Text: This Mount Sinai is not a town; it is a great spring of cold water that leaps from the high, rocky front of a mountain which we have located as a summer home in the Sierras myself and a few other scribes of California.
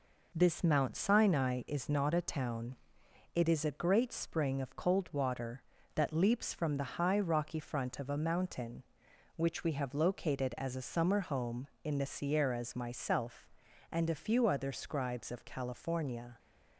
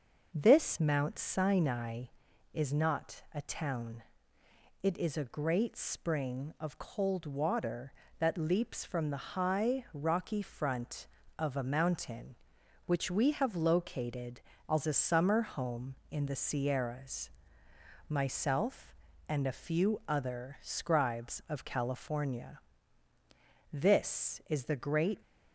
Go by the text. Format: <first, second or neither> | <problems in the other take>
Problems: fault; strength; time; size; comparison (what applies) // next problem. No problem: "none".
first | pauses between "Sierras" and "myself"; noticeable; at 17.3 s; 0.76 s long // goes on to say "This is the great"; from 23.7 s on; 1.4 s long